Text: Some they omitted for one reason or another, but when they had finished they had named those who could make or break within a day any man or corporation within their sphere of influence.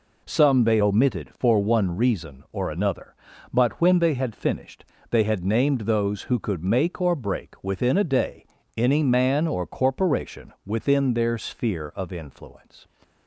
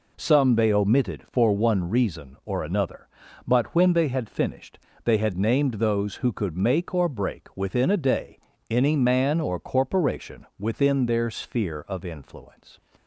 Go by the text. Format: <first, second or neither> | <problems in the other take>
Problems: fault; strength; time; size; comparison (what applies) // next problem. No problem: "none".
neither | pauses between "finished" and "they"; slight; the same in both // pauses between "day" and "any"; slight; the same in both